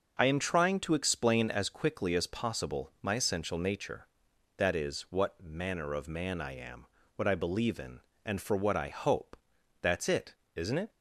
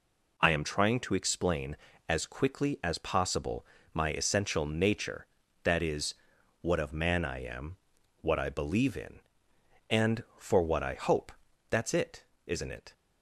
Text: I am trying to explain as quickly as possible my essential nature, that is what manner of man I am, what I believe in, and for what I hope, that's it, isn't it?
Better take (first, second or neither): first